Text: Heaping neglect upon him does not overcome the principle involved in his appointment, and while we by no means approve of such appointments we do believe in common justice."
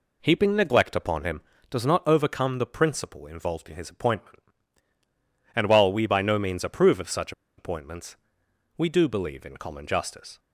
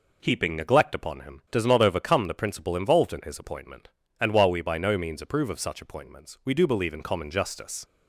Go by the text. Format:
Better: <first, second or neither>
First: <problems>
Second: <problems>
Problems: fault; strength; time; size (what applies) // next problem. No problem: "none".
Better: second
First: pauses between "such" and "appointments"; slight; at 7.3 s; 0.26 s long // pauses between "appointments" and "we"; noticeable; at 8.1 s; 0.62 s long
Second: none